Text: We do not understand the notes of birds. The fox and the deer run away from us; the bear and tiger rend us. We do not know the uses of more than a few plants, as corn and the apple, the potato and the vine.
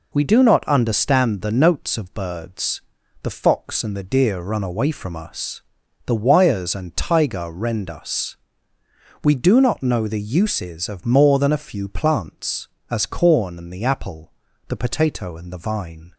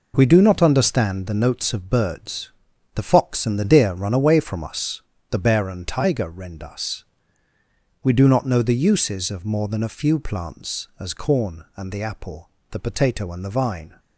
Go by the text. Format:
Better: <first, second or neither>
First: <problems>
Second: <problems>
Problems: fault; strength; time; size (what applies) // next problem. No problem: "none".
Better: second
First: says "wires" for "bear"; at 6.1 s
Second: none